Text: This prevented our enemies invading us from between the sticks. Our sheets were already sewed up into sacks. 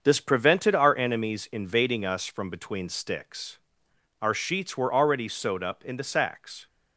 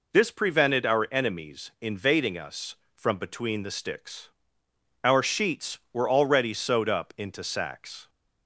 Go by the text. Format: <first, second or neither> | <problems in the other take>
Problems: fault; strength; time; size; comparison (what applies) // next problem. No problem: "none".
second | starts louder than the rest; until 1.0 s; 6.5 dB // skips "the"; at 2.8 s